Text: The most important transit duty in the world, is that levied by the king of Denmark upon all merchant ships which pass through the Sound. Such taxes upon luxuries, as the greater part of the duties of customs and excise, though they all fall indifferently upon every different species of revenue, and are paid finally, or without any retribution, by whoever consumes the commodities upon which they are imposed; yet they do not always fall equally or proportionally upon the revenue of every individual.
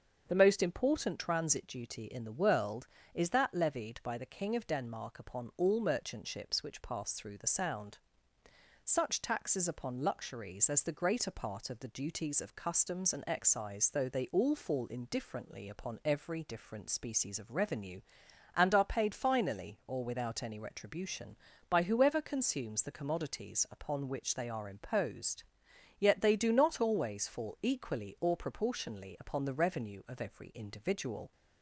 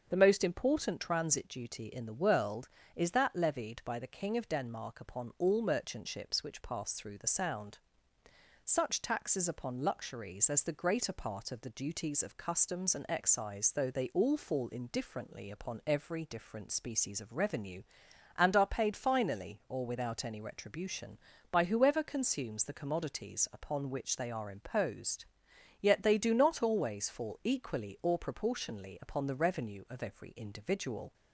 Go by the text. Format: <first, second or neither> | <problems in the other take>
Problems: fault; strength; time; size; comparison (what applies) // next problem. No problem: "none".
neither | starts louder than the rest; the same in both